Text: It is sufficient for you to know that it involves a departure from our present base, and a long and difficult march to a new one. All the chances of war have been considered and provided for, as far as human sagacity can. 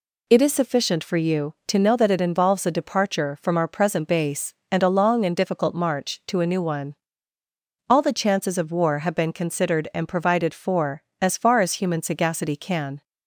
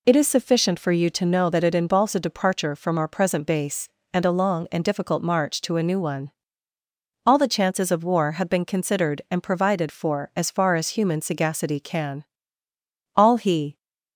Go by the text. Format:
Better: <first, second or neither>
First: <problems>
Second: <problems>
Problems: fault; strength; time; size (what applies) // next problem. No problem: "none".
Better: first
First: none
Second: goes on to say "All he"; noticeable; from 13.1 s on; 0.62 s long